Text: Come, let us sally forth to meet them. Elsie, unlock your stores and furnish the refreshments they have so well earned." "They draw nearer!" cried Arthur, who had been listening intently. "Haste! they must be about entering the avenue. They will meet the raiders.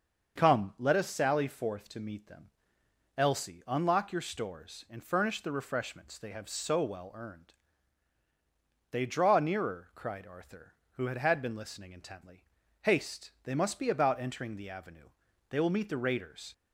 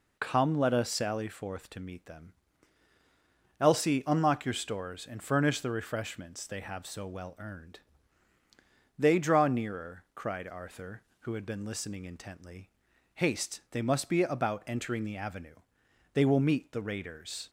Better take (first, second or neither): second